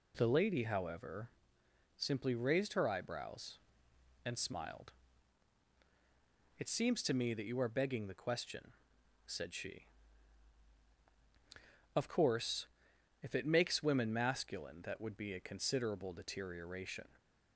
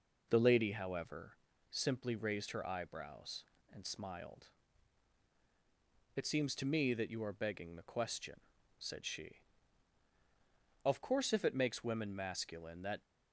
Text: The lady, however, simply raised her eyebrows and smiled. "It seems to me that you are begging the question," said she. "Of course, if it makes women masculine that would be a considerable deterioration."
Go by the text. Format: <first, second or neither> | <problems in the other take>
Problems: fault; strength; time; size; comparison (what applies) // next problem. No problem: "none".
first | stops before "would be a considerable deterioration"; at 13.0 s